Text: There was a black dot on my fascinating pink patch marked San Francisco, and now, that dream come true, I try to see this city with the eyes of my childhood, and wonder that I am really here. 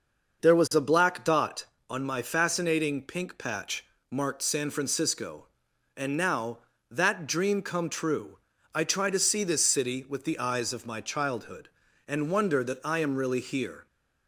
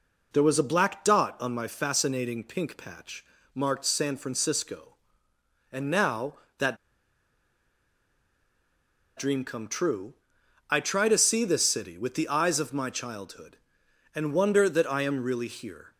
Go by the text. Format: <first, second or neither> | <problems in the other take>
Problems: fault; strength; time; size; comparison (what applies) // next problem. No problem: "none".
first | pauses between "patch" and "marked"; slight; at 3.2 s; 0.30 s long; slight in the first // pauses between "that" and "dream"; strong; at 6.7 s; 2.4 s long